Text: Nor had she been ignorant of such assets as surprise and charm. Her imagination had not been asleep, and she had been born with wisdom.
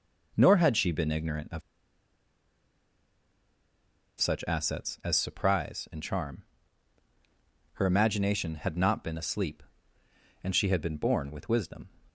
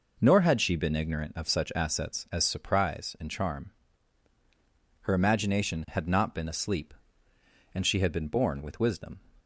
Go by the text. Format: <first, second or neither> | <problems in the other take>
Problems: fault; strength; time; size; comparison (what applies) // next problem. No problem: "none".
second | pauses between "of" and "such"; strong; at 1.6 s; 2.5 s long